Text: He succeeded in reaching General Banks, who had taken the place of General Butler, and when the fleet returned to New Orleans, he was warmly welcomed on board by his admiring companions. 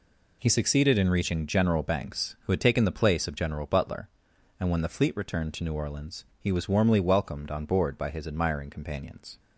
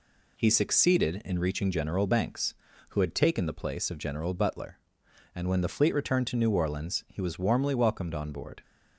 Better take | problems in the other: first | stops before "by his admiring companions"; at 8.6 s

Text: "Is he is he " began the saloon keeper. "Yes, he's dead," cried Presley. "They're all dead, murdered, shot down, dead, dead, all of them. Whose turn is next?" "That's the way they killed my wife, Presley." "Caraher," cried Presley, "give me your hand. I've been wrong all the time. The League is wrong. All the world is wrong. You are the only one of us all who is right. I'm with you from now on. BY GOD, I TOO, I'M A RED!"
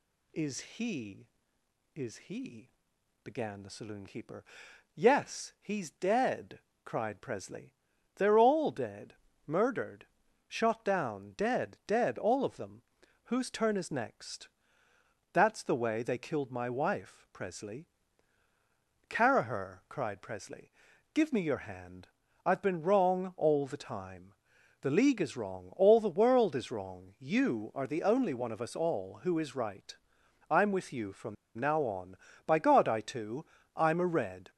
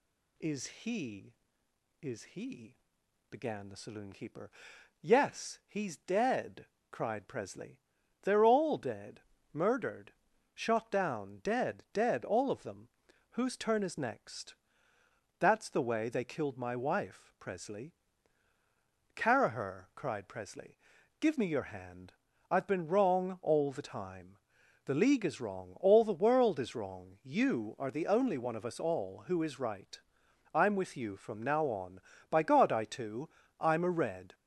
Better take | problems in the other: second | pauses between "from" and "now"; slight; at 31.3 s; 0.22 s long

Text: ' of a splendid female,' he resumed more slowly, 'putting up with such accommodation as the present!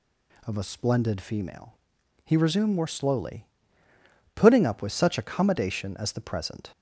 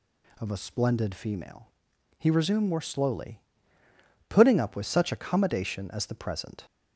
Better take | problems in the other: neither | none

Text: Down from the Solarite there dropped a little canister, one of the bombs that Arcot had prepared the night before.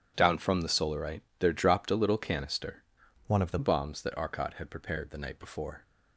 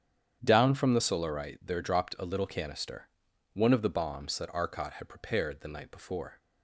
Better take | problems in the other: second | starts louder than the rest; strong; until 1.1 s; 9 dB; strong in the second // pauses between "Solarite" and "there"; slight; at 1.2 s; 0.16 s long // changes voice from "one" to "the"; from 3.2 to 3.5 s; 0.3 s long

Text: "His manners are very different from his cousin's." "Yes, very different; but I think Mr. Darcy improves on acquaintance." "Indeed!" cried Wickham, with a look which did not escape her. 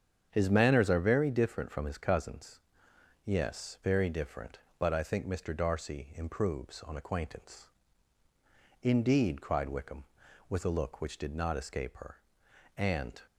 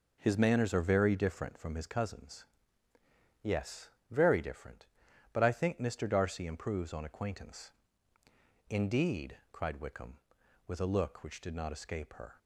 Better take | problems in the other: second | starts louder than the rest; strong; until 1.3 s; 8 dB // goes on to say "And"; slight; from 12.7 s on; 0.42 s long

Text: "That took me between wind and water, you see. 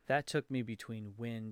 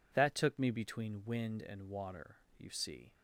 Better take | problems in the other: second | stops before "and water you see"; at 1.4 s

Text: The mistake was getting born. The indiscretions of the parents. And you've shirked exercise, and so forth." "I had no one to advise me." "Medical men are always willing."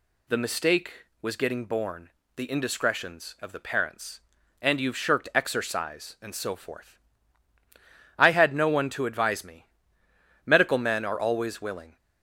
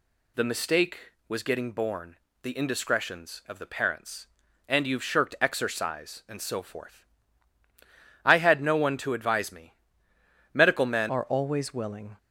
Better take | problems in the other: first | changes voice at "are"; from 11.0 s on; 1.1 s long

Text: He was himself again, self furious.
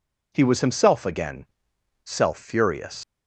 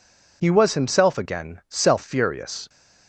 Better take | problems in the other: second | leaves "furious" unfinished; at 3.0 s; 135 ms

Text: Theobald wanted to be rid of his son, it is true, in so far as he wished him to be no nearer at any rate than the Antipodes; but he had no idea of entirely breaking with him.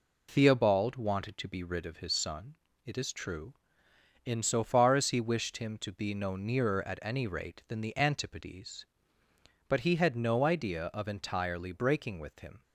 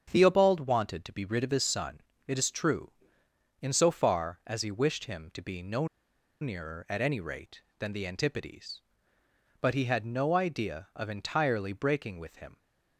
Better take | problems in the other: first | starts louder than the rest; strong; until 1.1 s; 7.5 dB // pauses between "no" and "nearer"; noticeable; at 5.8 s; 0.54 s long

